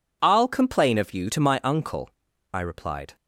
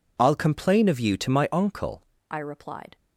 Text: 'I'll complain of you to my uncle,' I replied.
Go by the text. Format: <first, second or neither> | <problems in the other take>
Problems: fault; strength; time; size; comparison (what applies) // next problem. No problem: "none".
first | changes voice at "I"; from 2.3 s on; 0.6 s long